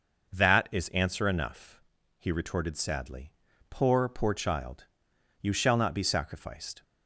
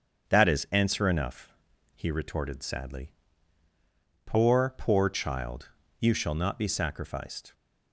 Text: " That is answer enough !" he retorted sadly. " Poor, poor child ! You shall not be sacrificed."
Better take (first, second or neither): neither